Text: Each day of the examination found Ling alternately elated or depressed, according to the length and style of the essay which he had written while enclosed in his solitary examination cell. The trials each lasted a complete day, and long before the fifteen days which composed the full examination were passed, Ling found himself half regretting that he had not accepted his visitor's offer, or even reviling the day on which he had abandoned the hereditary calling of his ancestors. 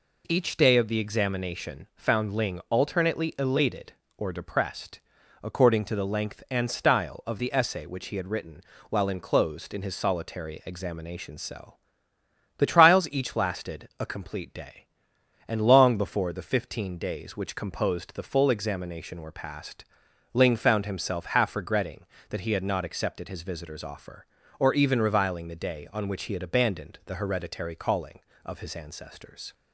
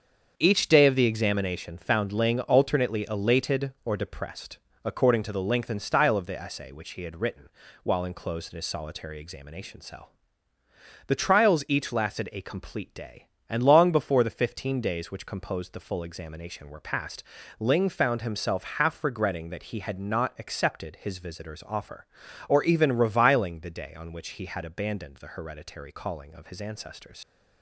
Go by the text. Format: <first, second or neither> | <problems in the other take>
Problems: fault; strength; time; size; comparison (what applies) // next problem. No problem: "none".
first | starts louder than the rest; strong; until 1.3 s; 7 dB // pauses between "written" and "while"; slight; at 7.4 s; 0.36 s long; slight in the first // leaves "ancestors" unfinished; at 27.2 s; 85 ms